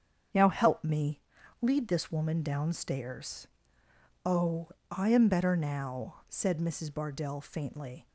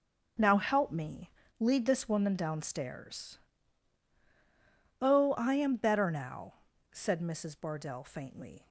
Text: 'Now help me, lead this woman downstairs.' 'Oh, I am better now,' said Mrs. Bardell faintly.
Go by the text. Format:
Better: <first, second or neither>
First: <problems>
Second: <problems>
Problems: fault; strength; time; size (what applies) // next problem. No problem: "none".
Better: neither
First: starts louder than the rest; strong; until 1.7 s; 7.5 dB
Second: starts louder than the rest; until 1.6 s; 6.5 dB